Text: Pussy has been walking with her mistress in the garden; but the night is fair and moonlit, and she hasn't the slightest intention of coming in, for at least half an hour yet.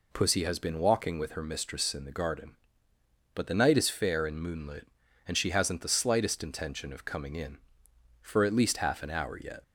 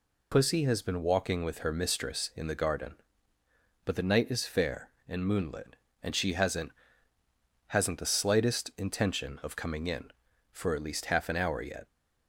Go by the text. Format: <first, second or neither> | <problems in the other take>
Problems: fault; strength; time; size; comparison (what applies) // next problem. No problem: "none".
first | says "hasn't" twice; at 7.6 s